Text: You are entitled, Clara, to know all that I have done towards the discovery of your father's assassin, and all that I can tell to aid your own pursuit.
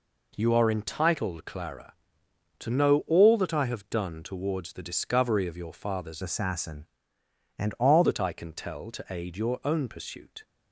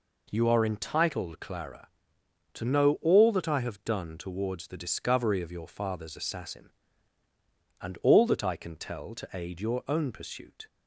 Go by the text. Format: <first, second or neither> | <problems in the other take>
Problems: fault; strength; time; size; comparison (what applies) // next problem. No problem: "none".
second | changes voice from "assassin" to "all"; from 6.2 to 8.0 s; 1.8 s long